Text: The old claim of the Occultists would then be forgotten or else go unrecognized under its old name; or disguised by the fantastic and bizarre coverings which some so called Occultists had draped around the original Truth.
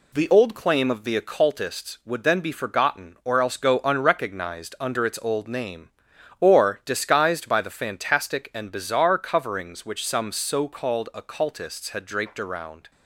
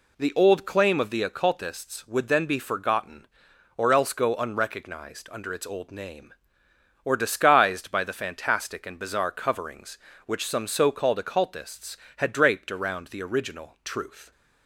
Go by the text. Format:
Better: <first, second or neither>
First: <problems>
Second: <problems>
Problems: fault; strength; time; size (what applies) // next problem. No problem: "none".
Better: second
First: stops before "the original Truth"; at 12.9 s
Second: none